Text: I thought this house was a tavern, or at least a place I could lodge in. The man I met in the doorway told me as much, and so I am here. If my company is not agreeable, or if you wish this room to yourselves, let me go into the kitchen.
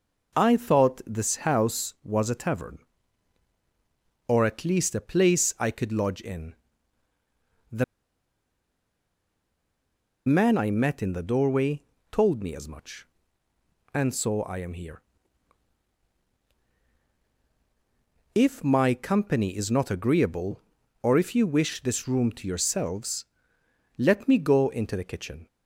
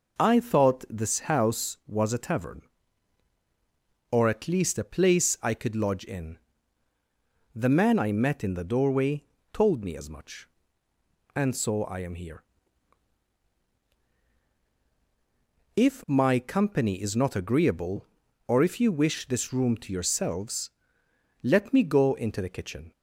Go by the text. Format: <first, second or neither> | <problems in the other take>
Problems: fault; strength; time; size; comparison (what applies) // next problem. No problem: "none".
second | pauses between "The" and "man"; strong; at 7.8 s; 2.4 s long // pauses between "doorway" and "told"; slight; at 11.8 s; 0.28 s long; slight in the second